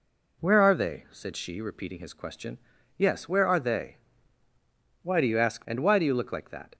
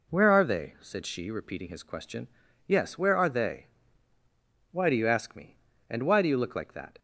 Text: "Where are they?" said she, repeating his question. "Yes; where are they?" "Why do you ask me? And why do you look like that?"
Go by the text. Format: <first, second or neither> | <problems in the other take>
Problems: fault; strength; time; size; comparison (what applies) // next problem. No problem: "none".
second | skips "me"; at 5.6 s